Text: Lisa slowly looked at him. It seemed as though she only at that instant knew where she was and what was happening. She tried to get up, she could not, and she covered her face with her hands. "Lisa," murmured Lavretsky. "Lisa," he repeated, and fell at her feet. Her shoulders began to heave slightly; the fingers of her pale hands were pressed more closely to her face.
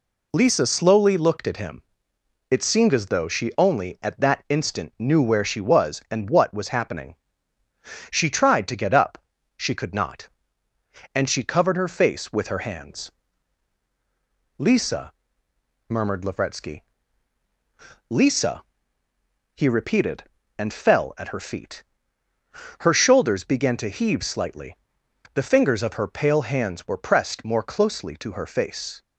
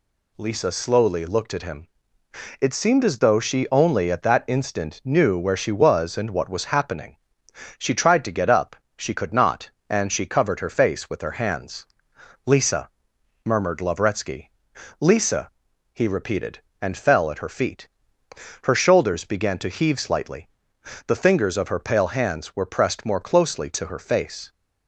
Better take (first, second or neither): neither